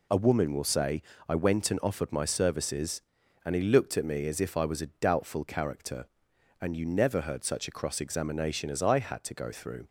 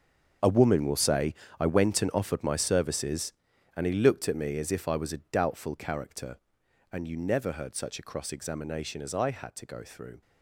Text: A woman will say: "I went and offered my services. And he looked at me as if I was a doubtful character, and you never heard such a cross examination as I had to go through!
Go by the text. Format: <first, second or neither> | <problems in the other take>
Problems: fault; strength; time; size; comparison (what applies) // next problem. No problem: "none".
first | gets quieter; strong; throughout; 14.5 dB